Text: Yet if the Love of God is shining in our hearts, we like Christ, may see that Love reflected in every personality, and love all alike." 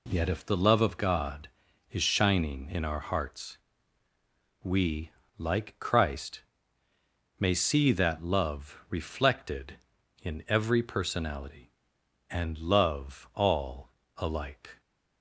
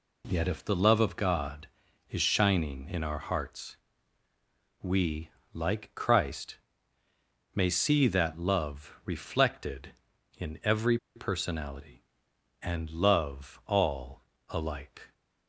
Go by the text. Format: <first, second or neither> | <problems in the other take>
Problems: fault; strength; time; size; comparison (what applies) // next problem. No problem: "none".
first | pauses between "we" and "like"; slight; at 5.2 s; 0.24 s long; slight in the first // pauses between "every" and "personality"; slight; at 10.9 s; 0.17 s long // pauses between "all" and "alike"; slight; at 14.2 s; 0.26 s long; slight in the first